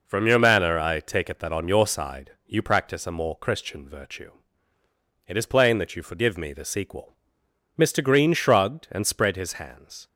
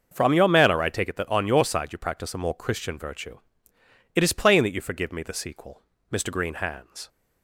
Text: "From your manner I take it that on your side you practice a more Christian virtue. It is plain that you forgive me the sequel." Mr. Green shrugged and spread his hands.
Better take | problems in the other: first | starts louder than the rest; until 1.1 s; 6 dB // skips "shrugged and spread his"; at 6.5 s

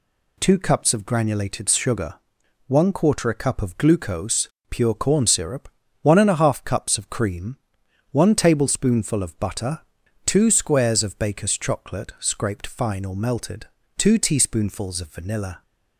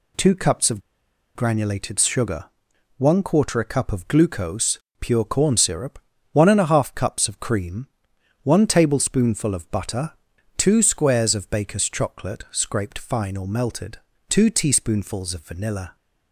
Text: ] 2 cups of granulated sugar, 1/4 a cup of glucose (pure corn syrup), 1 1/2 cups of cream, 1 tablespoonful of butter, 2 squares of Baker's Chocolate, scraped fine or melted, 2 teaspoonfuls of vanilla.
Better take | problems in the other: first | pauses between "of" and "granulated"; noticeable; at 0.8 s; 0.53 s long

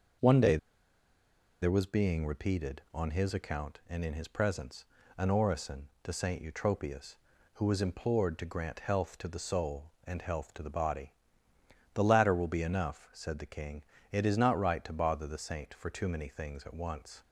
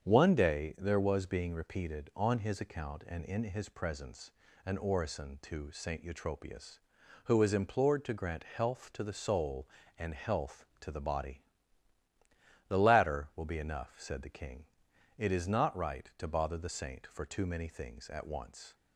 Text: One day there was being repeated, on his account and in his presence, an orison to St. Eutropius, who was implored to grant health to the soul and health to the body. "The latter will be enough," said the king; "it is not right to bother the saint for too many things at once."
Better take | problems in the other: second | starts louder than the rest; until 2.2 s; 6.5 dB; strong in the second // pauses between "day" and "there"; at 0.5 s; 1.0 s long

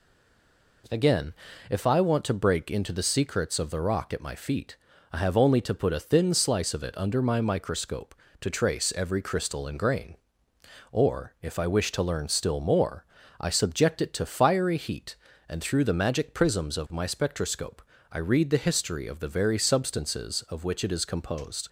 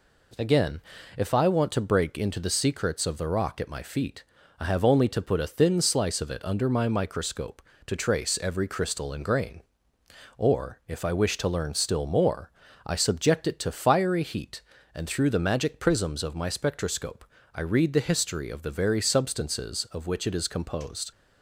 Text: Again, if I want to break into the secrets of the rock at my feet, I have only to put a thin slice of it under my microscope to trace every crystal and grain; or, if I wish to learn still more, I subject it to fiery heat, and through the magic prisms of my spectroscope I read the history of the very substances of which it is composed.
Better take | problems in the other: second | stays silent before the first word; slight; until 0.8 s; 0.8 s long // pauses between "spectroscope" and "I"; slight; at 17.8 s; 0.28 s long; slight in the second

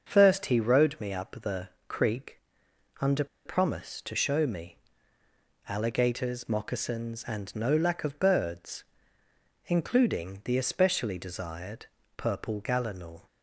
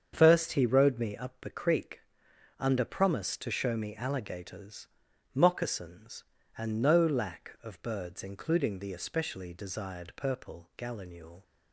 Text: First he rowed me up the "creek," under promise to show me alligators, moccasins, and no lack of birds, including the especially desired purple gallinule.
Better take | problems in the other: second | starts louder than the rest; until 1.1 s; 6.5 dB; strong in the second // pauses between "the" and "creek"; slight; at 1.6 s; 0.22 s long // pauses between "under" and "promise"; slight; at 3.2 s; 0.19 s long // pauses between "me" and "alligators"; noticeable; at 4.7 s; 0.90 s long // pauses between "desired" and "purple"; slight; at 11.8 s; 0.32 s long

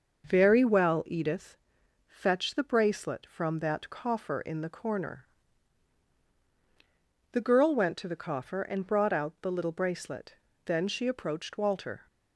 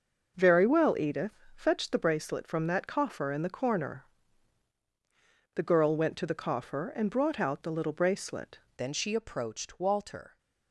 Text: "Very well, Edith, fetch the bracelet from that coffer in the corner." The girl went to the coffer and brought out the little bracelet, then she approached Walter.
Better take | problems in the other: first | starts louder than the rest; noticeable; until 1.3 s; 6 dB; noticeable in the first // changes voice at "then"; from 8.7 s on; 1.6 s long

